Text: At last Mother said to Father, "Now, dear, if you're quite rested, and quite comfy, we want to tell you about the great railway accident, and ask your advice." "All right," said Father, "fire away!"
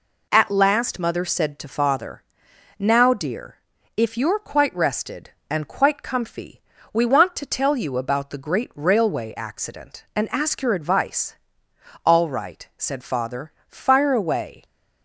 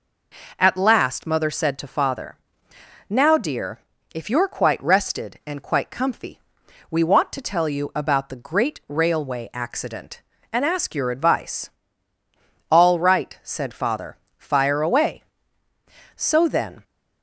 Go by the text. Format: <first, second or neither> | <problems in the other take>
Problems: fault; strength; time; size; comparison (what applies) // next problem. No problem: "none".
first | goes on to say "So then"; noticeable; from 16.1 s on; 0.68 s long